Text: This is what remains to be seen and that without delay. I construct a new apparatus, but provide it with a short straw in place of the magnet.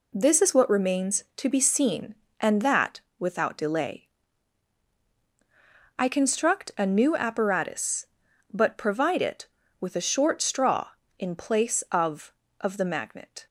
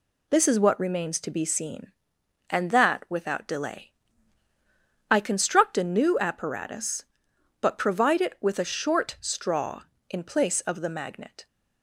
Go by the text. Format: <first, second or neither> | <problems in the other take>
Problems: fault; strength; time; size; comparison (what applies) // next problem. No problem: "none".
second | pauses between "that" and "without"; slight; at 2.9 s; 0.18 s long // says "of" twice; at 12.6 s